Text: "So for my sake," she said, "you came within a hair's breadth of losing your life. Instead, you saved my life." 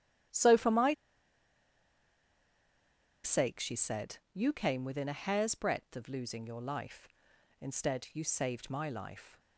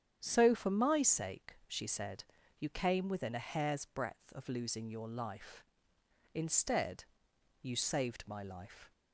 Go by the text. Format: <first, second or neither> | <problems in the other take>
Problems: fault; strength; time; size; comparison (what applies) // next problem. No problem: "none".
second | starts louder than the rest; strong; until 3.6 s; 12 dB; strong in the second // pauses between "my" and "sake"; strong; at 0.9 s; 2.3 s long